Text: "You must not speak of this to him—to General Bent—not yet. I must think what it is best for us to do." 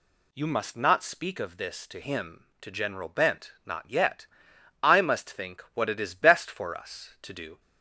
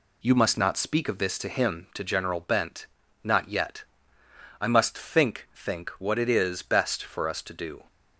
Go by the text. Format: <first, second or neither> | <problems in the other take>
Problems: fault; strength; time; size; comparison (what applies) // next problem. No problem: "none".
first | says "think" twice; at 5.5 s